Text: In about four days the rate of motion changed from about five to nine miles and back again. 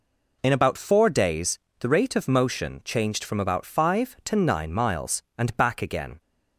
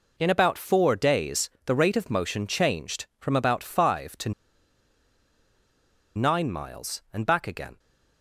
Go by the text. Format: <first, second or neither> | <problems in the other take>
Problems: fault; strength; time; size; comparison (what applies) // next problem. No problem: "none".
first | pauses between "days" and "the"; slight; at 1.5 s; 0.16 s long; slight in the first // pauses between "to" and "nine"; strong; at 4.3 s; 1.8 s long